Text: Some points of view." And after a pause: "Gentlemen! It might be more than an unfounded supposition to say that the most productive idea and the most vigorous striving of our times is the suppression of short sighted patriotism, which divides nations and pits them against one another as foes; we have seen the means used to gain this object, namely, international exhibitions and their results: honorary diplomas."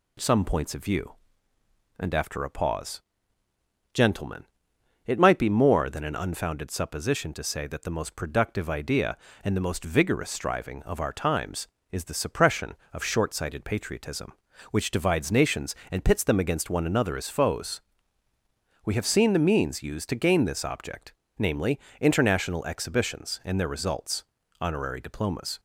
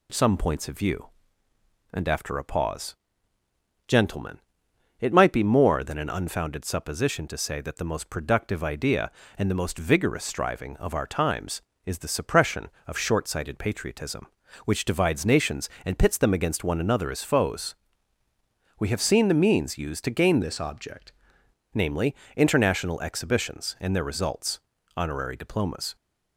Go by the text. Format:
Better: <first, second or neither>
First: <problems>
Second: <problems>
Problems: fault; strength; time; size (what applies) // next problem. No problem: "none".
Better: first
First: none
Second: changes voice from "this" to "object"; from 20.4 to 21.1 s; 0.7 s long